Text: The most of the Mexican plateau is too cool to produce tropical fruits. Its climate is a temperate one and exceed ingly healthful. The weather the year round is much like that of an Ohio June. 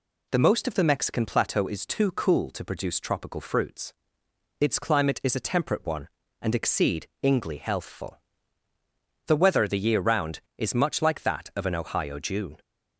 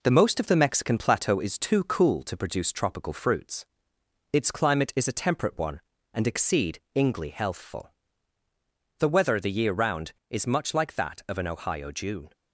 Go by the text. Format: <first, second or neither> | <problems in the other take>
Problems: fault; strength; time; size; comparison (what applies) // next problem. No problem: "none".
first | gets quieter; slight; throughout; 2 dB // pauses between "exceed" and "ingly"; slight; at 6.7 s; 0.18 s long; slight in the first